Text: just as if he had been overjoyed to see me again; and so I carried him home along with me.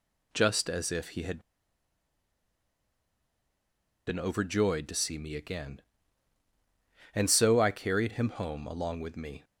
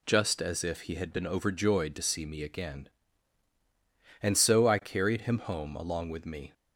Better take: second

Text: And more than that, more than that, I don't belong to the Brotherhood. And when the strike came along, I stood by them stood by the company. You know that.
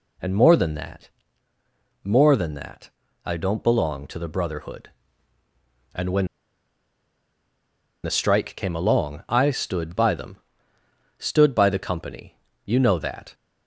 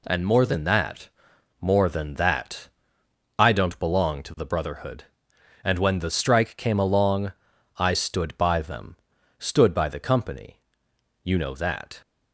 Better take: second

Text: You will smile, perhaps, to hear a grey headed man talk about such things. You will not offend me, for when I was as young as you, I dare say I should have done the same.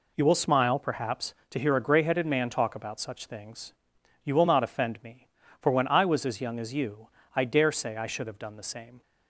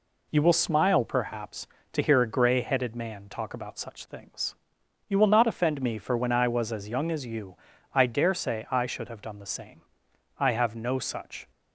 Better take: first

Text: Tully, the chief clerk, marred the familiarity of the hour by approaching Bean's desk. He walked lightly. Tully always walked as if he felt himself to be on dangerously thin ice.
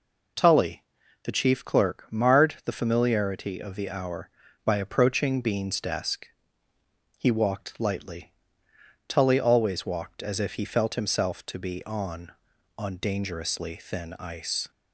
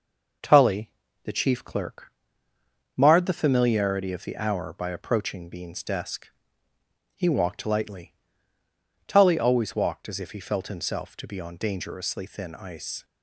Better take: second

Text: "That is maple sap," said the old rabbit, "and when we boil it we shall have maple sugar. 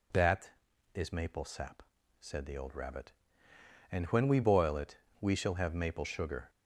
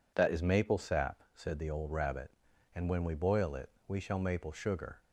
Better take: first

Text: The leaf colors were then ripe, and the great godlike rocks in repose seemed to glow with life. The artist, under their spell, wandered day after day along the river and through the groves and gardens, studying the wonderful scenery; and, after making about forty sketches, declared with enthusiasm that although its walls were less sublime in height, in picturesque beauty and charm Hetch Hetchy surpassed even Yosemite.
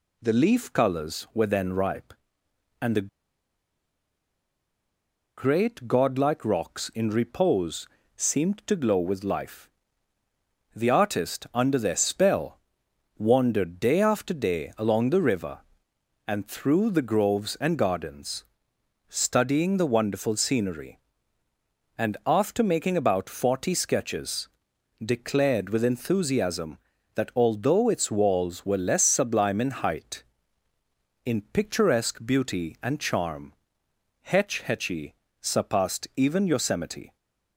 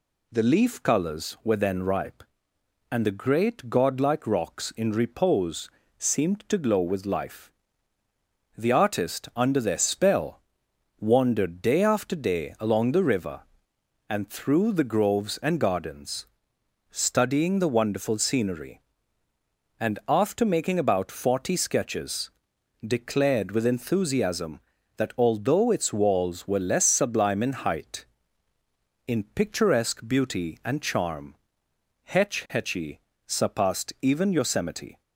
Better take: second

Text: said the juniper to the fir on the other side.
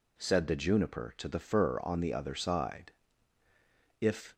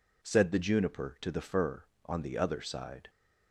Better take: second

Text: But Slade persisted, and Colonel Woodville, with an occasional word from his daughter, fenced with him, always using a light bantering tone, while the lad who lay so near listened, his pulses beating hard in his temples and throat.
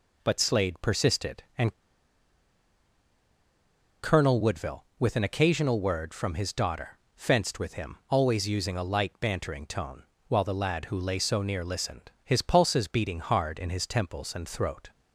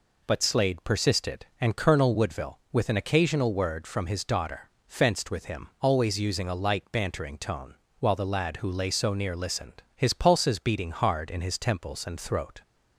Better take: second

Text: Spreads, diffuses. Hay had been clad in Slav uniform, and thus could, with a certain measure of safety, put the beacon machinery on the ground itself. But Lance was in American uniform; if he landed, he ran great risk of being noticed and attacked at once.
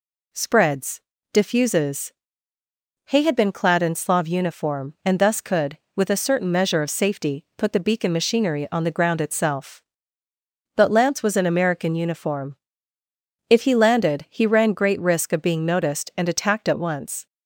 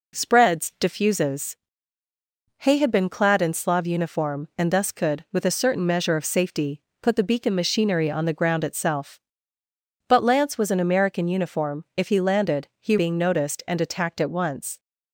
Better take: first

